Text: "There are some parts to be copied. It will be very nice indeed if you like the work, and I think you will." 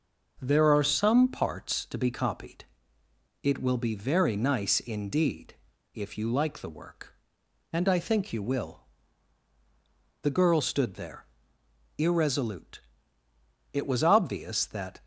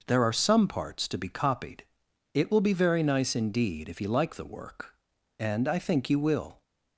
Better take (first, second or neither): second